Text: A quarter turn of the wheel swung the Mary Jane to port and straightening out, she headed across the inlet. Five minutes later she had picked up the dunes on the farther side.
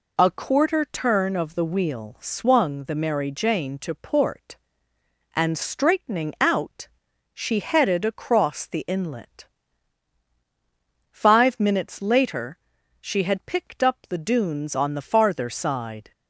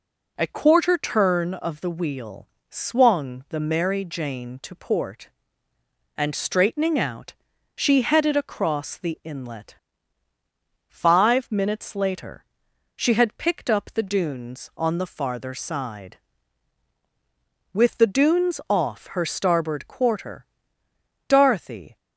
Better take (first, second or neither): first